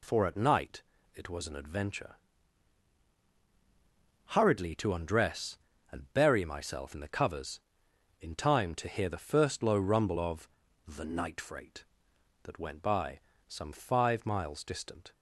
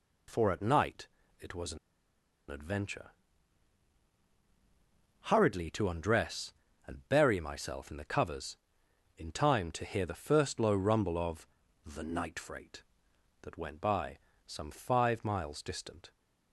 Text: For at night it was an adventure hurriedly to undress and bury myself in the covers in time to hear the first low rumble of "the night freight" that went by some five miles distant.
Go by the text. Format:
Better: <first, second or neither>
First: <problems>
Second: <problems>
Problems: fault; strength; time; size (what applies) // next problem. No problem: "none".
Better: first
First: pauses between "night" and "it"; slight; at 0.8 s; 0.32 s long // pauses between "adventure" and "hurriedly"; strong; at 2.1 s; 2.2 s long // pauses between "of" and "the"; at 10.4 s; 0.38 s long // pauses between "by" and "some"; slight; at 13.1 s; 0.28 s long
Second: pauses between "night" and "it"; slight; at 1.0 s; 0.32 s long // pauses between "an" and "adventure"; noticeable; at 1.7 s; 0.72 s long // pauses between "adventure" and "hurriedly"; strong; at 3.1 s; 2.2 s long // pauses between "of" and "the"; at 11.4 s; 0.38 s long // pauses between "by" and "some"; slight; at 14.1 s; 0.28 s long